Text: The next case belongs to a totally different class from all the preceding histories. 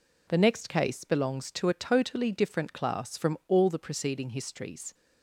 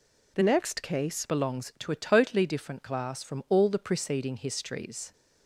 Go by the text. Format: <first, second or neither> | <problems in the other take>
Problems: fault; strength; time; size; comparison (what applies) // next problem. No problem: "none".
first | changes voice from "next" to "case"; from 0.4 to 1.2 s; 0.8 s long